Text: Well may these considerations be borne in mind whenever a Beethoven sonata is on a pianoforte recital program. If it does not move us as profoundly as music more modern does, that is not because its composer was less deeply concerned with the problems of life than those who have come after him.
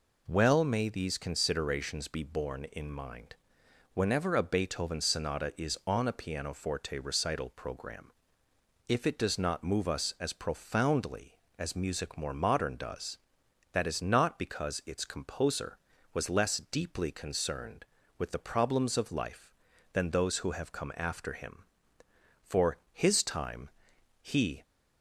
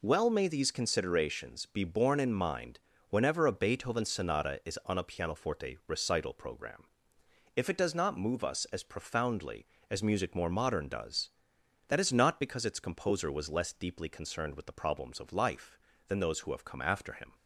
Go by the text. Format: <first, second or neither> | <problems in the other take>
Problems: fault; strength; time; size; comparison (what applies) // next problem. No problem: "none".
second | pauses between "mind" and "whenever"; noticeable; at 3.3 s; 0.58 s long; slight in the second // goes on to say "For his time he"; strong; from 22.4 s on; 2.1 s long